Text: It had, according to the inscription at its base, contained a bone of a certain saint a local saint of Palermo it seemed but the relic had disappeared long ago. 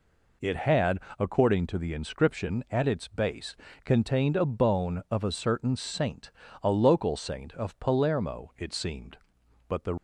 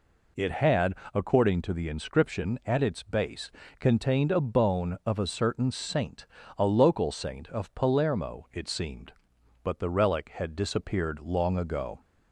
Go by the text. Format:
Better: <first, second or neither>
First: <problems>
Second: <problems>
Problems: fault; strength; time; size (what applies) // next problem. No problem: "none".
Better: second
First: pauses between "saint" and "a"; slight; at 6.3 s; 0.32 s long // stops before "relic had disappeared long ago"; at 9.9 s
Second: pauses between "saint" and "a"; slight; at 6.2 s; 0.32 s long